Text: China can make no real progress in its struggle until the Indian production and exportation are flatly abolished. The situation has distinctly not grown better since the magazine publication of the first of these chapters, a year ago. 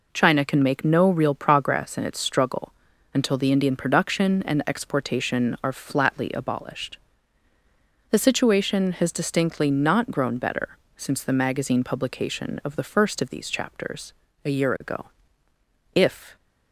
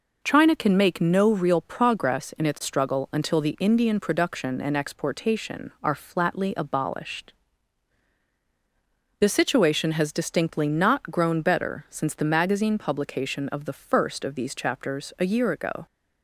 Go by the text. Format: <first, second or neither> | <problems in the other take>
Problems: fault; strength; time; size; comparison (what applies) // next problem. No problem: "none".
second | pauses between "struggle" and "until"; at 2.7 s; 0.42 s long // pauses between "better" and "since"; slight; at 10.7 s; 0.20 s long // goes on to say "If"; slight; from 15.9 s on; 0.42 s long